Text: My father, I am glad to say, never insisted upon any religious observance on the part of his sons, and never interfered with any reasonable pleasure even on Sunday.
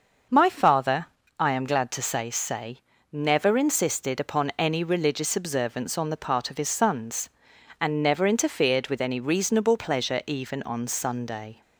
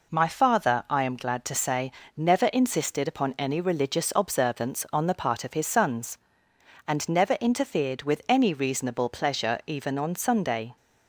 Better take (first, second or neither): second